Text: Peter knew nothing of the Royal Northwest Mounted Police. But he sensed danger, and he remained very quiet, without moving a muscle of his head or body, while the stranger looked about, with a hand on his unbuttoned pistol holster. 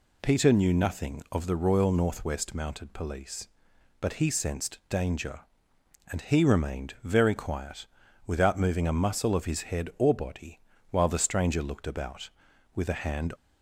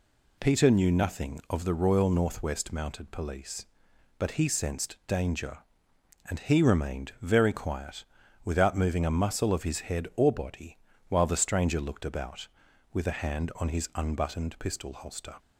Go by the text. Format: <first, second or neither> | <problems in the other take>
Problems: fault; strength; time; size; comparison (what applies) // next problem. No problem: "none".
second | stops before "on his unbuttoned pistol holster"; at 13.3 s